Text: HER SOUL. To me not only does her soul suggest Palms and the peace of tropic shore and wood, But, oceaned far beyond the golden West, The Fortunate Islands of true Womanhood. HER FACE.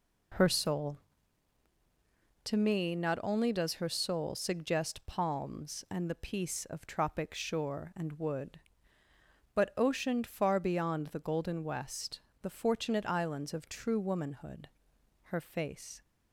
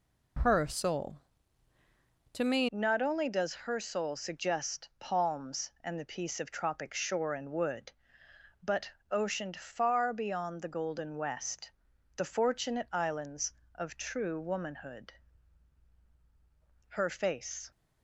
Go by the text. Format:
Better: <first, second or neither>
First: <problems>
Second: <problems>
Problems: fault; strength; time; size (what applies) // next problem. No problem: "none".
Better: first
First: none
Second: changes voice at "not"; from 2.7 s on; 15.0 s long